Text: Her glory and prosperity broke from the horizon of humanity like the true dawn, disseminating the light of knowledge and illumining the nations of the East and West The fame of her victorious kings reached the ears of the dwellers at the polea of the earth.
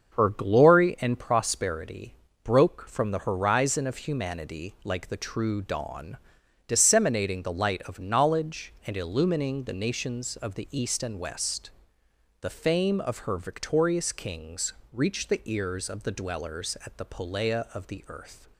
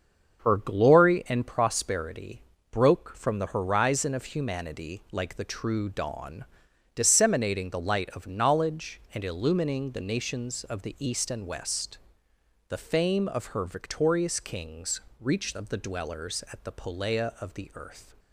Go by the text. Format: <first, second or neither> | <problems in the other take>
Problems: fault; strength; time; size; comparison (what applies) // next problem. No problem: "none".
first | starts louder than the rest; until 1.4 s; 6.5 dB; also in the first // pauses between "prosperity" and "broke"; slight; at 2.4 s; 0.28 s long; slight in the first // pauses between "West" and "The"; noticeable; at 11.9 s; 0.70 s long; noticeable in the first // pauses between "kings" and "reached"; slight; at 14.9 s; 0.20 s long; slight in the first // skips "the ears"; at 15.5 s